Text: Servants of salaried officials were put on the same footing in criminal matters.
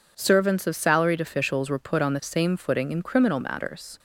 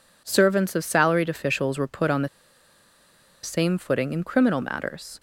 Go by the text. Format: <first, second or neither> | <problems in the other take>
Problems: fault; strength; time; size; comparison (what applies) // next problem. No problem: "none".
first | pauses between "the" and "same"; at 2.2 s; 1.1 s long